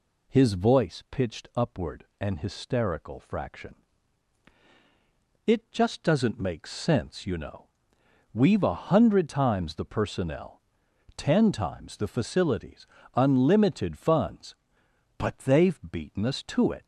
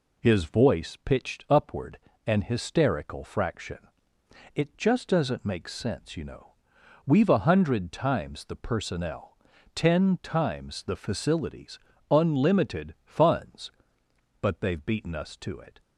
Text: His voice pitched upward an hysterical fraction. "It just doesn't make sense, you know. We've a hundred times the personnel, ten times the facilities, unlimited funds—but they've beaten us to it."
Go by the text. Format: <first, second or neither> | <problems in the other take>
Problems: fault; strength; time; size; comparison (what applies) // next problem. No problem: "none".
neither | pauses between "upward" and "an"; slight; the same in both